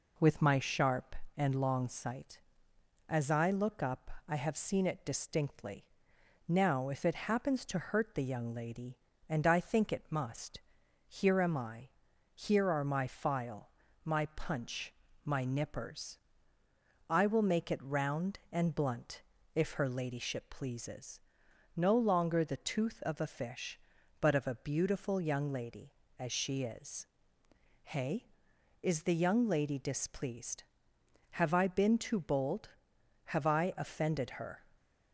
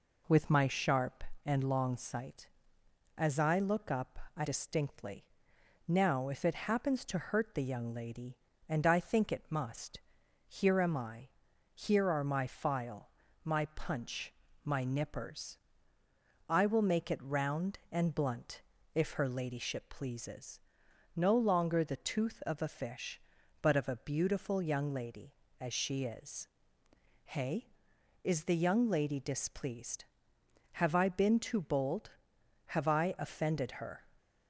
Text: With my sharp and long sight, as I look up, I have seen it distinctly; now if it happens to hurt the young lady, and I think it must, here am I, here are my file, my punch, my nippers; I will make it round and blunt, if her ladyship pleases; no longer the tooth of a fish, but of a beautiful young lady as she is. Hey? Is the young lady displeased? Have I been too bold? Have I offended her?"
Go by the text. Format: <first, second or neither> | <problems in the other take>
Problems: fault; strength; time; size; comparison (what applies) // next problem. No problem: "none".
first | skips "have seen it"; at 4.4 s